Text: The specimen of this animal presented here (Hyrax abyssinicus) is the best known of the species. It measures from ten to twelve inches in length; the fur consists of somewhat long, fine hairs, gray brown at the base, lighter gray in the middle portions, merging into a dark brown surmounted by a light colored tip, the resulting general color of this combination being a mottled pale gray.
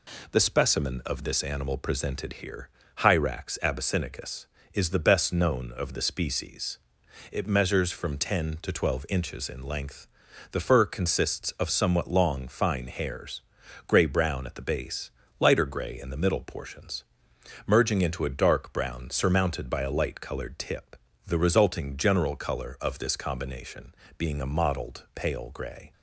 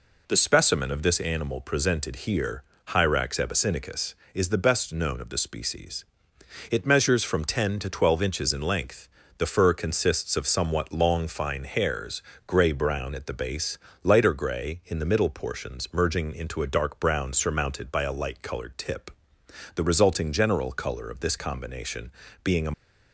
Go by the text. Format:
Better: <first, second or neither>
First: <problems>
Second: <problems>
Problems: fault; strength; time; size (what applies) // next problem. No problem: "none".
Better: first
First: pauses between "combination" and "being"; slight; at 23.9 s; 0.22 s long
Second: pauses between "combination" and "being"; slight; at 22.1 s; 0.32 s long // stops before "mottled pale gray"; at 22.7 s